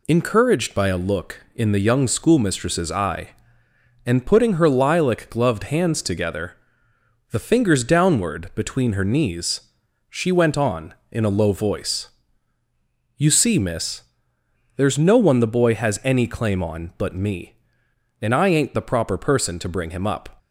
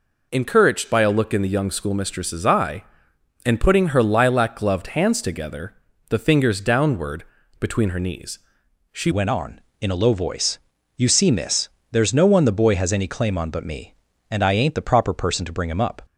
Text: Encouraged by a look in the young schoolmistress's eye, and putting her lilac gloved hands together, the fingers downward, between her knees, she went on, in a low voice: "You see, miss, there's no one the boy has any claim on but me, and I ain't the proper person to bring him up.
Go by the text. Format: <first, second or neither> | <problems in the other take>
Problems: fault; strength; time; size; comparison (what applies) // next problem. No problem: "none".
first | changes voice at "went"; from 9.1 s on; 6.9 s long